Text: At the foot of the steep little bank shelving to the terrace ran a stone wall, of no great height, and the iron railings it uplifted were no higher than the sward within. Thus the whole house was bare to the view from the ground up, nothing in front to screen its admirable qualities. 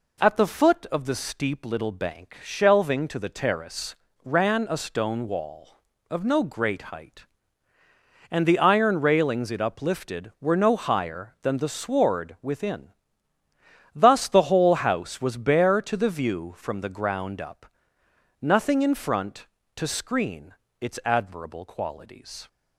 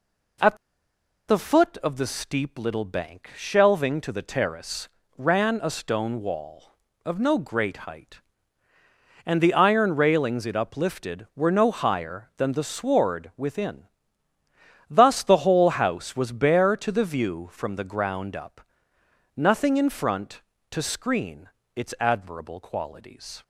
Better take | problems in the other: first | pauses between "At" and "the"; noticeable; at 0.5 s; 0.73 s long // pauses between "terrace" and "ran"; slight; at 4.8 s; 0.32 s long; slight in the first // pauses between "screen" and "its"; slight; at 21.4 s; 0.26 s long; slight in the first

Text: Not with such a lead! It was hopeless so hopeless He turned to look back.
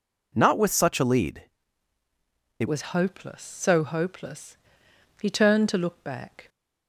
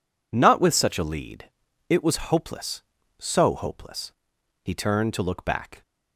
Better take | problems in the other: second | changes voice at "was"; from 2.6 s on; 3.8 s long // pauses between "hopeless" and "He"; noticeable; at 4.5 s; 0.64 s long; noticeable in the second

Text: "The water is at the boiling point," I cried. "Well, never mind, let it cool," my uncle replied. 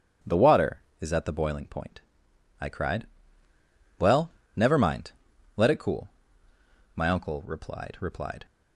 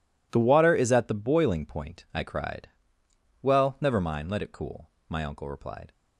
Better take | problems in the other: second | starts louder than the rest; until 1.4 s; 7 dB // says "replied" twice; at 7.9 s

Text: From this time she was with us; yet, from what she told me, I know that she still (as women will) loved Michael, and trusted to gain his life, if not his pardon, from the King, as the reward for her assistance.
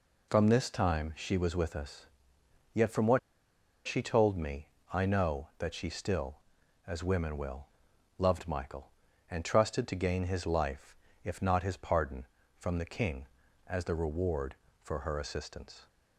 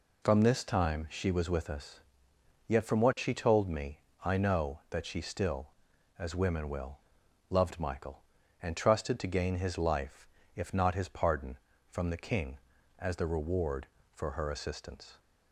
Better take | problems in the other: second | pauses between "what" and "she"; noticeable; at 3.1 s; 0.68 s long

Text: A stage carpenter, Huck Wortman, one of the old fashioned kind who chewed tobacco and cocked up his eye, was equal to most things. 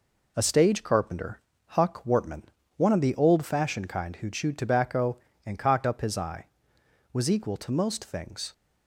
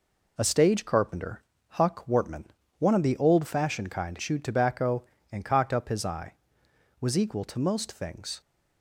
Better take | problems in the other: first | skips "who"; at 4.1 s

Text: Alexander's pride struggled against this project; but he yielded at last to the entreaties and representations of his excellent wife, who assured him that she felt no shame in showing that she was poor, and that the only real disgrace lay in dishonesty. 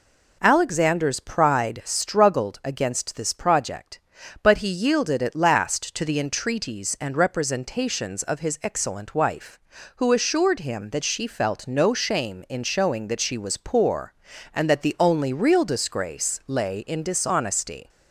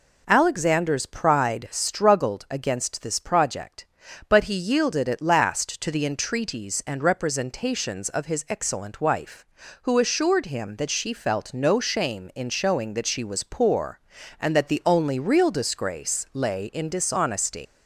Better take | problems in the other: first | leaves "dishonesty" unfinished; at 17.6 s; 95 ms

